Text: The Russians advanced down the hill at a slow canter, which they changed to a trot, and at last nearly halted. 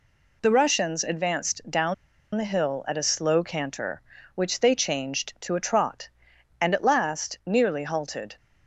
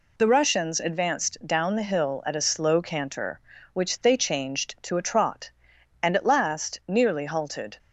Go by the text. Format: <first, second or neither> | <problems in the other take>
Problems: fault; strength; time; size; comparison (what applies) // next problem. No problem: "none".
second | pauses between "down" and "the"; at 1.9 s; 0.40 s long